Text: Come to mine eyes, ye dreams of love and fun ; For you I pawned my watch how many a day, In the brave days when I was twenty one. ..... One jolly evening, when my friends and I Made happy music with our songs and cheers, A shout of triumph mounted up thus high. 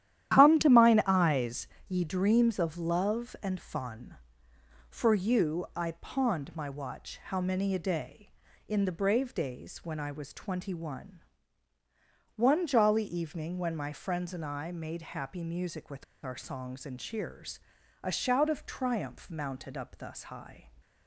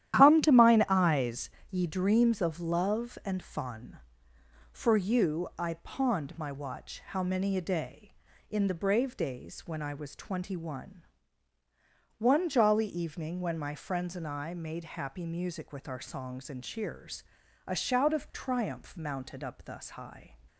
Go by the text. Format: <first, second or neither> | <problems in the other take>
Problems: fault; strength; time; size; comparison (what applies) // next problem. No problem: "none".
second | starts louder than the rest; strong; until 1.3 s; 11.5 dB; strong in the second // pauses between "with" and "our"; slight; at 16.0 s; 0.20 s long